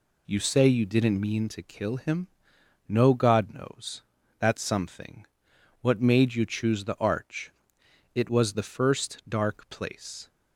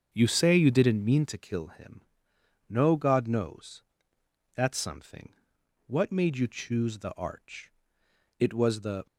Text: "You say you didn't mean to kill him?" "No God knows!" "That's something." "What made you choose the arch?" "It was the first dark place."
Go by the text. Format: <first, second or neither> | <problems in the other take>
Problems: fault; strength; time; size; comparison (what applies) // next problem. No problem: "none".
first | starts louder than the rest; until 1.1 s; 6.5 dB // stops before "first dark place"; at 9.0 s